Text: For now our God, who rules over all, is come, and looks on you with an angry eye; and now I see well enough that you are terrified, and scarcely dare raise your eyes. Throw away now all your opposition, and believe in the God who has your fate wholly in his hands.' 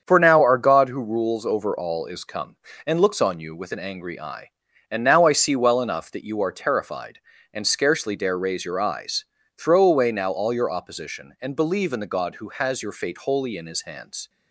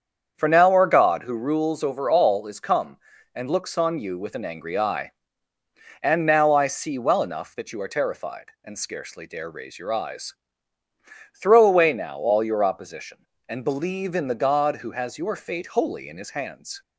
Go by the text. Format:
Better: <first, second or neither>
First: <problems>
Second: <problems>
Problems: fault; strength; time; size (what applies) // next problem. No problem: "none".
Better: neither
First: starts louder than the rest; strong; until 1.0 s; 7.5 dB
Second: starts louder than the rest; strong; until 1.3 s; 7.5 dB